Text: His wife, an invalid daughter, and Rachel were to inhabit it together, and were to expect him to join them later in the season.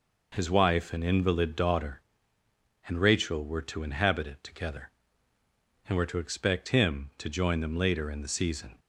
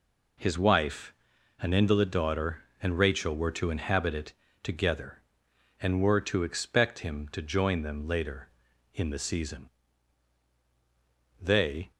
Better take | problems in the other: first | pauses between "it" and "together"; slight; at 4.3 s; 0.30 s long // goes on to say "They"; from 11.4 s on; 0.50 s long

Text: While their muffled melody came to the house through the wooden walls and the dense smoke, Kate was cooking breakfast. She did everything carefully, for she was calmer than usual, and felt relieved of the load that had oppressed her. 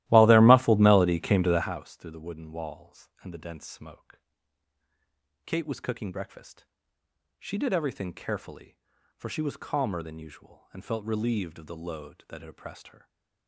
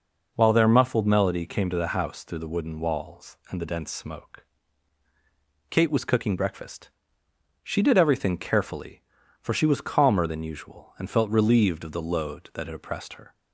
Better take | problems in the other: second | starts louder than the rest; strong; until 1.7 s; 15.5 dB // stays silent after the last word; slight; from 12.9 s on; 0.5 s long

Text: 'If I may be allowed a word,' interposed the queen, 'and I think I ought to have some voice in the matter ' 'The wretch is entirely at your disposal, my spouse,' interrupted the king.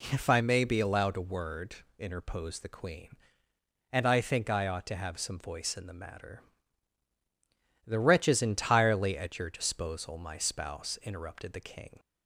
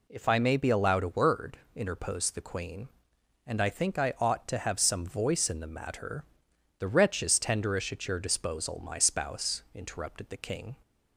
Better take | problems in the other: first | says "tenderish" for "entirely"; at 7.3 s

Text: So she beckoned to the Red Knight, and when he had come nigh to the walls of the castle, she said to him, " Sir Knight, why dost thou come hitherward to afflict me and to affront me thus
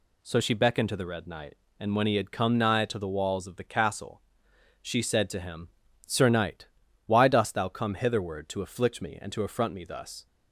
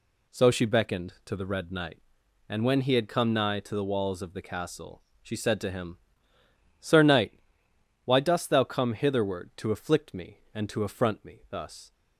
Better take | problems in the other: neither | none

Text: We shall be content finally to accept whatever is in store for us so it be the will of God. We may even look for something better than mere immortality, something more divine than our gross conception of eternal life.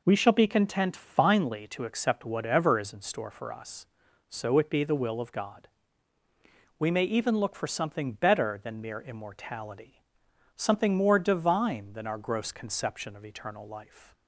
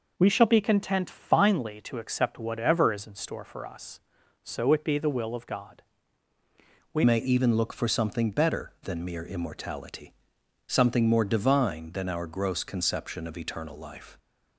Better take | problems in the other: first | changes voice at "may"; from 7.0 s on; 7.1 s long

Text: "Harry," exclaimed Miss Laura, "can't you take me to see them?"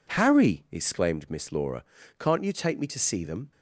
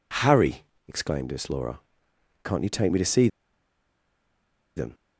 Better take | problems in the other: first | pauses between "see" and "them"; strong; at 3.2 s; 1.4 s long

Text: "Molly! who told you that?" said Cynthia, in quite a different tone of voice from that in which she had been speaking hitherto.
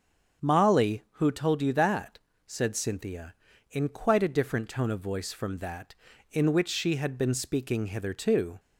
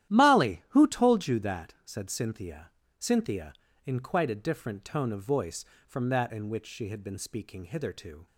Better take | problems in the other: first | starts louder than the rest; strong; until 1.1 s; 12 dB; strong in the first // says "Cynthia" twice; at 2.9 s

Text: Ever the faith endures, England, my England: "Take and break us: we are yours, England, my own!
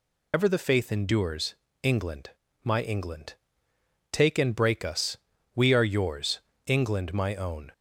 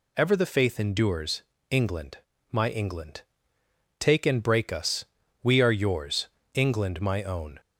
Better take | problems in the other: second | loses the start of "Ever"; at 0.3 s; 55 ms

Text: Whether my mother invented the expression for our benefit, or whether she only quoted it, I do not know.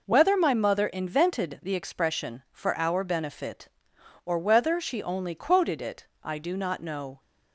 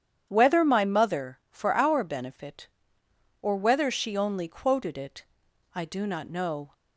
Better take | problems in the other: first | starts louder than the rest; strong; until 1.2 s; 9 dB // skips "invented the expression"; at 1.4 s

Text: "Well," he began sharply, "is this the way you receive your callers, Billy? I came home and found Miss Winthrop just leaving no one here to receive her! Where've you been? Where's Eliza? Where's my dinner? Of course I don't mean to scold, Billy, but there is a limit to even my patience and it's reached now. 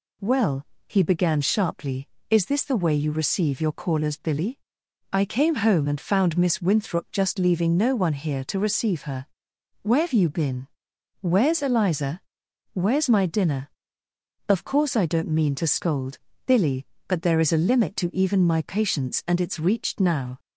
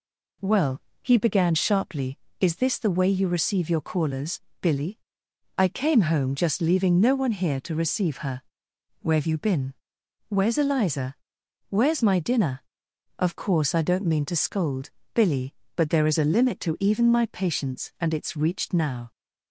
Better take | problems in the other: first | skips "and found Miss Winthrop"; at 6.3 s

